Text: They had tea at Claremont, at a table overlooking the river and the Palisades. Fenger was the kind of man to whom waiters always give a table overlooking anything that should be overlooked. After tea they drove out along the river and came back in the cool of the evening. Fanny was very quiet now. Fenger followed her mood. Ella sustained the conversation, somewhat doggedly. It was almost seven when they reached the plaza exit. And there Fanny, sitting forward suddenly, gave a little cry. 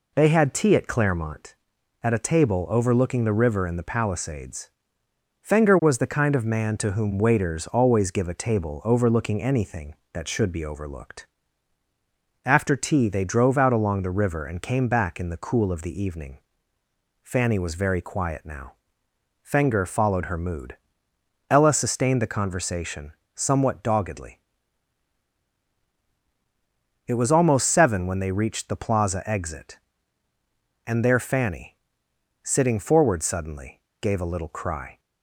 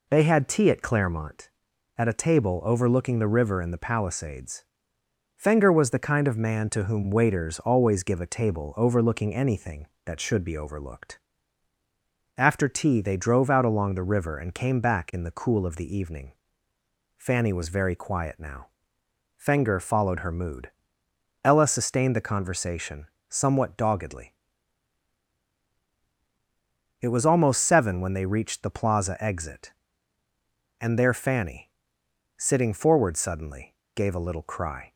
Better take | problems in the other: neither | none

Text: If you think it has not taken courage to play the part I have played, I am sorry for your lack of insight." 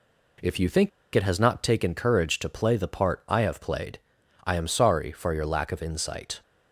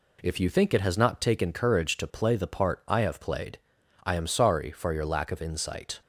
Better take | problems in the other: second | pauses between "think" and "it"; slight; at 0.9 s; 0.25 s long

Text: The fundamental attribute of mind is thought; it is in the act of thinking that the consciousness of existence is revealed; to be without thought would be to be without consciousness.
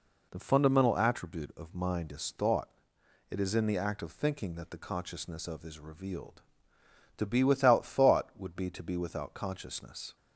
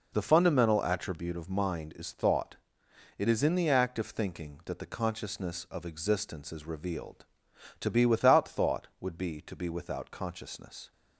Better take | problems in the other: second | skips "existence"; at 5.6 s

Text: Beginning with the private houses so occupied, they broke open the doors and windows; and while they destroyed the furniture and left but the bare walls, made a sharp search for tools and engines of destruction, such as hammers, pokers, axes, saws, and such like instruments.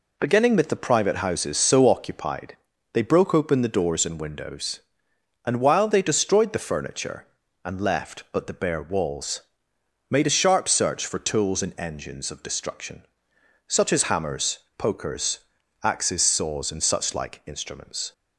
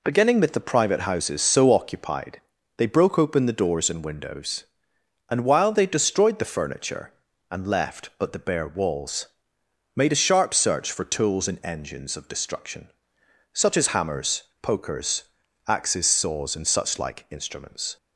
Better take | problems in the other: neither | none

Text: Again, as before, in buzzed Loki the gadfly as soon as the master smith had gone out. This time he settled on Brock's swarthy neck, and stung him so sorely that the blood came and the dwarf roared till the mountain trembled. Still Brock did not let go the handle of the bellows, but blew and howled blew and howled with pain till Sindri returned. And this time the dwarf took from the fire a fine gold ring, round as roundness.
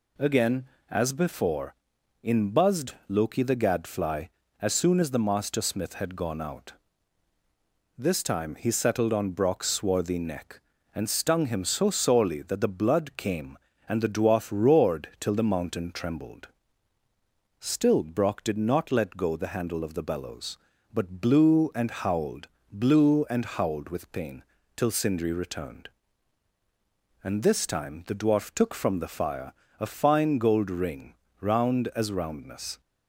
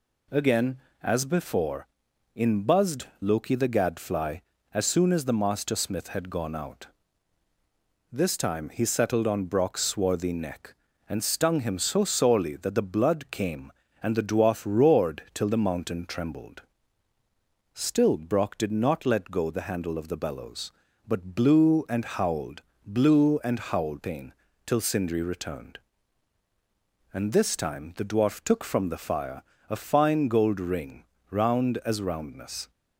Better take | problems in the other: first | pauses between "howled" and "blew"; slight; at 22.6 s; 0.24 s long; slight in the first // skips "with"; at 24.0 s // pauses between "pain" and "till"; slight; at 24.3 s; 0.32 s long; slight in the first // pauses between "fire" and "a"; slight; at 29.4 s; 0.26 s long; slight in the first

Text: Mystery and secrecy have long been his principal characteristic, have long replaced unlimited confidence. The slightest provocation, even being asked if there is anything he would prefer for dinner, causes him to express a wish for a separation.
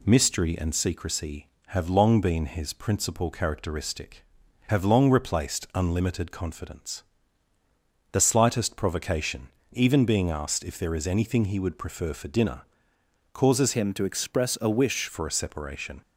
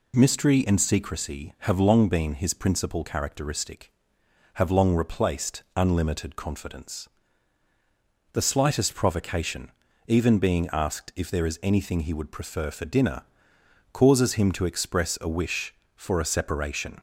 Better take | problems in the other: second | changes voice from "him" to "wish"; from 13.7 to 15.0 s; 1.3 s long

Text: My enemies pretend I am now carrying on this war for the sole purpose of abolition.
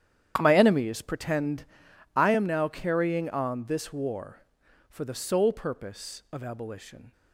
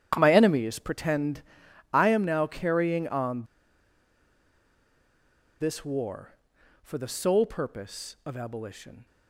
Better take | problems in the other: first | starts louder than the rest; strong; until 1.1 s; 10 dB; strong in the first // pauses between "pretend" and "I"; noticeable; at 1.4 s; 0.50 s long; noticeable in the first // pauses between "on" and "this"; strong; at 3.4 s; 2.1 s long

